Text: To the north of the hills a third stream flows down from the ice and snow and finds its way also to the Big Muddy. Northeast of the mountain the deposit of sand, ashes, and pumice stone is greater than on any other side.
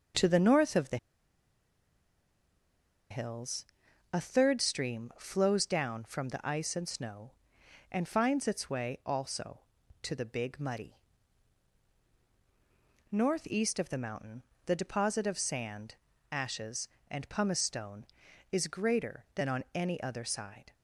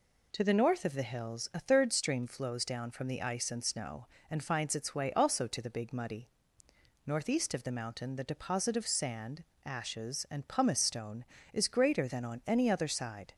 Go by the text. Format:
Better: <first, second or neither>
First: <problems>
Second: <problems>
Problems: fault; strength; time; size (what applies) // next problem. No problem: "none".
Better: second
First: starts louder than the rest; until 3.2 s; 6.5 dB // pauses between "the" and "hills"; strong; at 0.9 s; 2.1 s long // pauses between "hills" and "a"; noticeable; at 3.6 s; 0.46 s long // pauses between "mountain" and "the"; slight; at 14.4 s; 0.22 s long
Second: none